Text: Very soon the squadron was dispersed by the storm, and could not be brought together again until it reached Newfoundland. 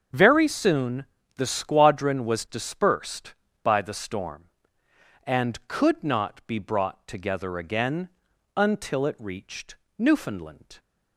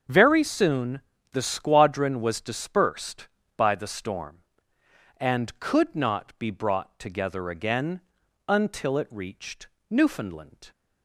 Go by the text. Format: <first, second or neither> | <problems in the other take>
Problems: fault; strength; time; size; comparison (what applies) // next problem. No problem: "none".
neither | starts louder than the rest; the same in both // pauses between "soon" and "the"; slight; the same in both // pauses between "again" and "until"; noticeable; the same in both // pauses between "reached" and "Newfoundland"; slight; the same in both